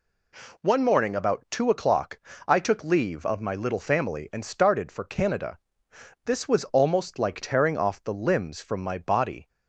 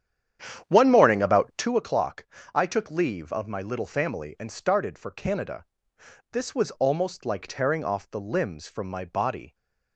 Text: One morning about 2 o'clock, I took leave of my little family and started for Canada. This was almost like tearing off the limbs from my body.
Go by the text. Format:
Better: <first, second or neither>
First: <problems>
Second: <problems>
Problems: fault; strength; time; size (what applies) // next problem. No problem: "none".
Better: first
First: none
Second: starts louder than the rest; strong; until 1.8 s; 9.5 dB